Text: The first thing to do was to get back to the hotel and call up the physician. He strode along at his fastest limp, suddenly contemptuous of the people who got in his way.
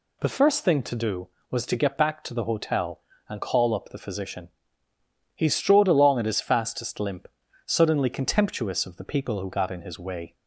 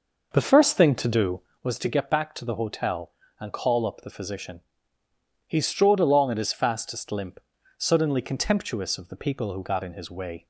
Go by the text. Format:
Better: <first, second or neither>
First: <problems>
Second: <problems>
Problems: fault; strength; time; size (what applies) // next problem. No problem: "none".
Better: first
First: none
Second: starts louder than the rest; noticeable; until 1.7 s; 5.5 dB